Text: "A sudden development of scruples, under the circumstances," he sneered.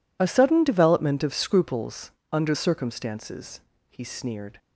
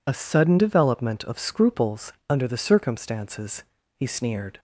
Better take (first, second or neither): second